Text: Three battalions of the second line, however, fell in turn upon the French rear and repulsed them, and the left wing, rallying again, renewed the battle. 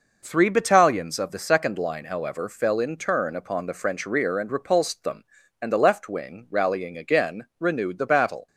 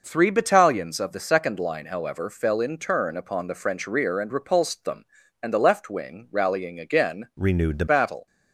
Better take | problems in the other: first | changes voice from "renewed" to "the"; from 7.3 to 7.8 s; 0.5 s long

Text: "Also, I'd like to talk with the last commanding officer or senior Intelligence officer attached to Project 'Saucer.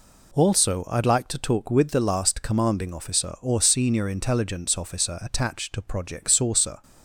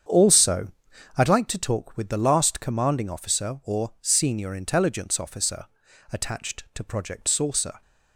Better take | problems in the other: first | starts louder than the rest; strong; until 1.4 s; 8 dB // pauses between "officer" and "attached"; noticeable; at 5.6 s; 0.48 s long

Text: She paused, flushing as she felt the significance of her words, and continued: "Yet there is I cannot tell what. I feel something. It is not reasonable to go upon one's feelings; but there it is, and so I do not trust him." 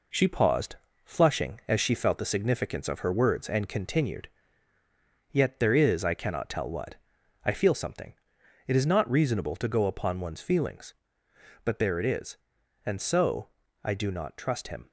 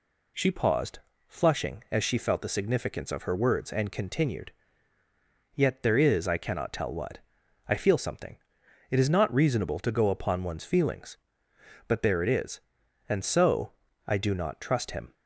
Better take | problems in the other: second | gets quieter; noticeable; throughout; 4.5 dB // pauses between "so" and "I"; slight; at 13.4 s; 0.36 s long; slight in the second

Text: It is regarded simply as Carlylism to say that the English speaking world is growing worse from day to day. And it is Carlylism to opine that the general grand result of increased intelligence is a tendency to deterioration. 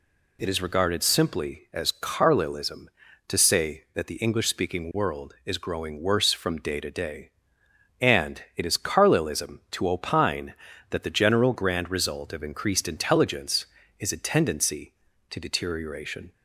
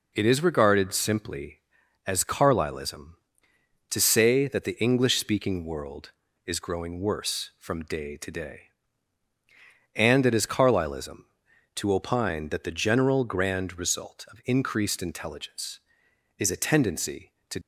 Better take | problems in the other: first | stops before "deterioration"; at 17.6 s

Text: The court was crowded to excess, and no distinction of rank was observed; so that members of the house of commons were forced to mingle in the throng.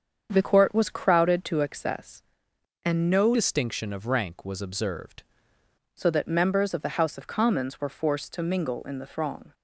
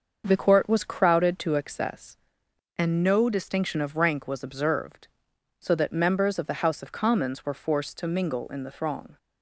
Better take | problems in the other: second | starts louder than the rest; strong; until 1.3 s; 7.5 dB; also in the second // changes voice from "distinction" to "observed"; from 3.3 to 5.2 s; 1.9 s long

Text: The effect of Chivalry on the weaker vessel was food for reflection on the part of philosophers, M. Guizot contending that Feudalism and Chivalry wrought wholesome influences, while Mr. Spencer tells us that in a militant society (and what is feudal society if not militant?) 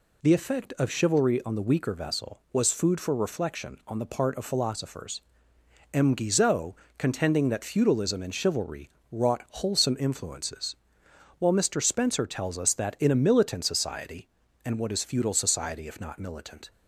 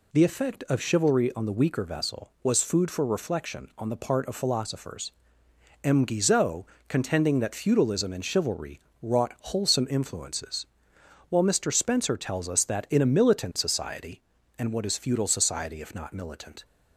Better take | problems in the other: neither | pauses between "Guizot" and "contending"; slight; the same in both // pauses between "Chivalry" and "wrought"; slight; the same in both

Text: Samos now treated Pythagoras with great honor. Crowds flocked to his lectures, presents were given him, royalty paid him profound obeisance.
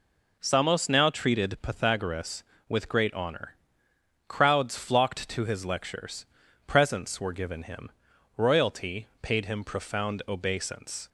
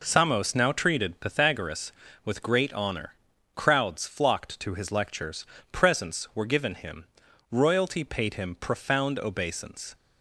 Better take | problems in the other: neither | none

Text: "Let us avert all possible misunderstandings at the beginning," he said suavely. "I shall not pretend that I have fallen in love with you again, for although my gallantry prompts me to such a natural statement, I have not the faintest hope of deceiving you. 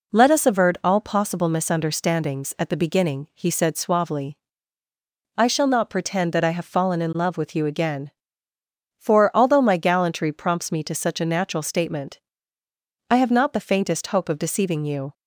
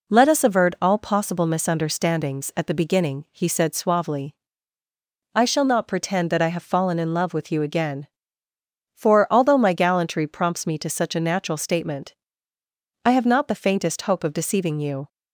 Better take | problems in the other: neither | none

